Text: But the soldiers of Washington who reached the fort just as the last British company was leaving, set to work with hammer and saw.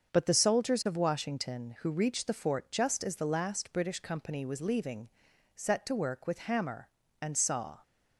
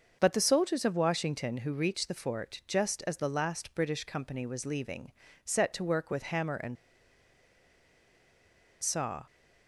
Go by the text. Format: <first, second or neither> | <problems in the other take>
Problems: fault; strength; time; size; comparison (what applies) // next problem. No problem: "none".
first | starts louder than the rest; until 1.2 s; 6.5 dB; also in the first // pauses between "and" and "saw"; strong; at 6.7 s; 2.0 s long